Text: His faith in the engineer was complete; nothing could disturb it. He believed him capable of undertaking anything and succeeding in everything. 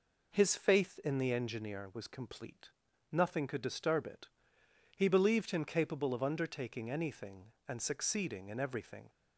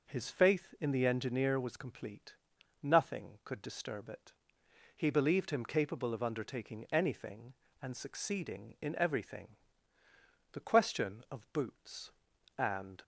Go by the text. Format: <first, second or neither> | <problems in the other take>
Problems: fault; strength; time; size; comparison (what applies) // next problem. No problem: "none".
first | goes on to say "The question of boots and"; strong; from 10.5 s on; 2.5 s long